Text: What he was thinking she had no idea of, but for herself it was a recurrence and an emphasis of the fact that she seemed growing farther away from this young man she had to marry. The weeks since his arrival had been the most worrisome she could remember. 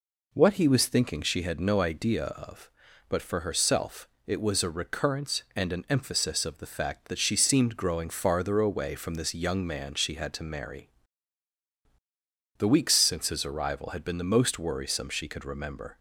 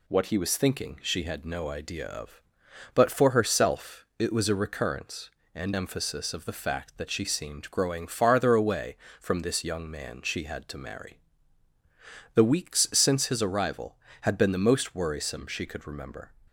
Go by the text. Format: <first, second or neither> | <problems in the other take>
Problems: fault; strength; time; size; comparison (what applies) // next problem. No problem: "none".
first | pauses between "herself" and "it"; slight; at 4.0 s; 0.16 s long; slight in the first // skips "an"; at 5.7 s